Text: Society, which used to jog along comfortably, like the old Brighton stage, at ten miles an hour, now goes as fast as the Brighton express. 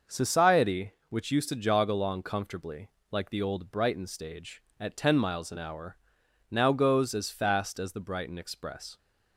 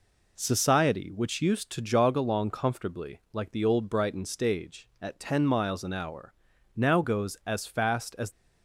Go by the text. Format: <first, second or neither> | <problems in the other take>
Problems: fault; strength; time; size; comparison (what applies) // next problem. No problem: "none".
first | stops before "the Brighton express"; at 8.3 s